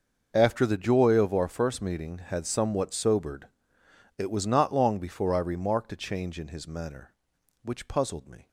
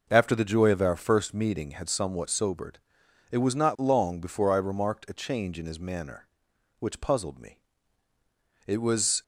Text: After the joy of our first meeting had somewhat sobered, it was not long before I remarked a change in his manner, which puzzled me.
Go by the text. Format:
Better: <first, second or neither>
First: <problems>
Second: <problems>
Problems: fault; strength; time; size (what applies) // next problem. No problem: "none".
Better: first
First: none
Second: goes on to say "It was"; from 8.6 s on; 0.56 s long